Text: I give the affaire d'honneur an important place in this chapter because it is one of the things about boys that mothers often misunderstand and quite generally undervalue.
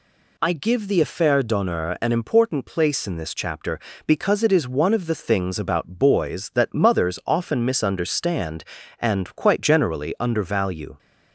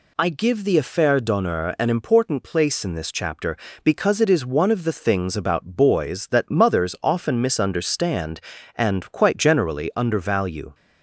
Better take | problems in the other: neither | none

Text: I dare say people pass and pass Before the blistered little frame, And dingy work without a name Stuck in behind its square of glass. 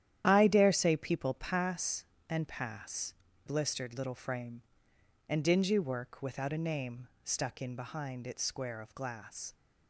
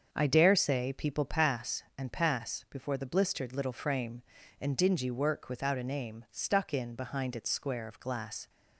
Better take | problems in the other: second | starts louder than the rest; strong; until 1.2 s; 10.5 dB; also in the second // skips "Before the"; at 3.2 s // pauses between "name" and "Stuck"; slight; at 7.0 s; 0.16 s long

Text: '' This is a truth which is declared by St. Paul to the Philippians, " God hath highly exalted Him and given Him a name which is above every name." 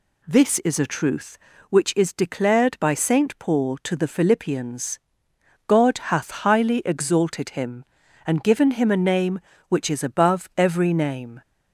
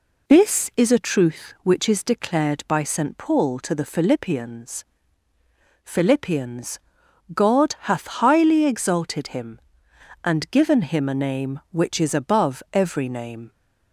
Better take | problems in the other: first | says "Philippians" twice; at 5.8 s

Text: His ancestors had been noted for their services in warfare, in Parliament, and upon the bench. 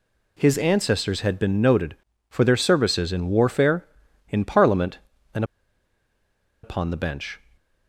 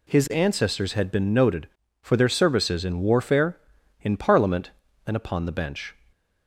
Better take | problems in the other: second | pauses between "and" and "upon"; at 5.4 s; 1.1 s long

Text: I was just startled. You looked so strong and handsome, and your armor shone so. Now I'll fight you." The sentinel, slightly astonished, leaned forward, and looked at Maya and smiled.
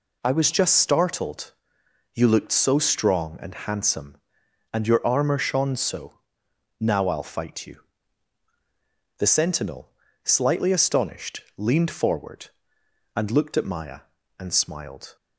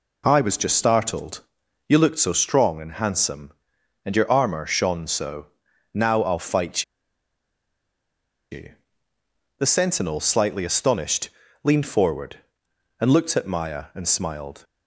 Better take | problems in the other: first | pauses between "fight" and "you"; strong; at 6.8 s; 1.6 s long

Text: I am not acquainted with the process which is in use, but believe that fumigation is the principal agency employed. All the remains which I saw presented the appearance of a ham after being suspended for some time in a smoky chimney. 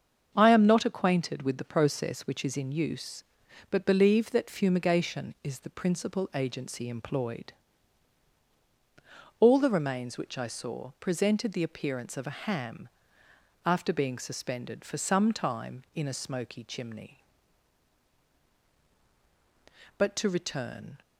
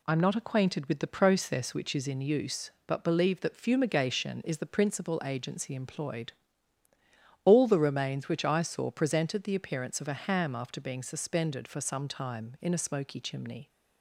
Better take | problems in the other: second | starts louder than the rest; until 1.3 s; 7 dB // pauses between "ham" and "after"; noticeable; at 12.8 s; 0.76 s long // goes on to say "But to return"; noticeable; from 19.9 s on; 1.0 s long

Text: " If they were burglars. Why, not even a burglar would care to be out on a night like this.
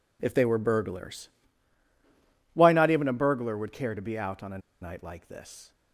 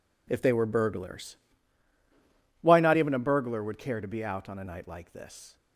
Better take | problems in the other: second | pauses between "a" and "night"; slight; at 4.5 s; 0.22 s long

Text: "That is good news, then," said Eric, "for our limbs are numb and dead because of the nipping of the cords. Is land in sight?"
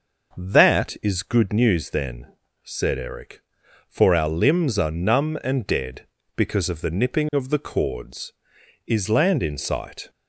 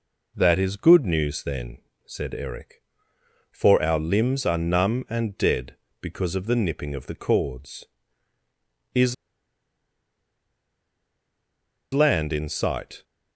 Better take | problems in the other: first | pauses between "Is" and "land"; strong; at 9.1 s; 2.8 s long

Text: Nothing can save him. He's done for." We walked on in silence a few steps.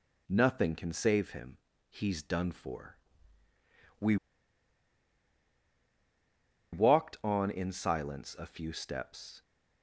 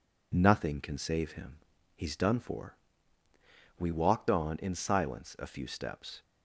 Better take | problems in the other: second | pauses between "We" and "walked"; strong; at 4.1 s; 2.5 s long

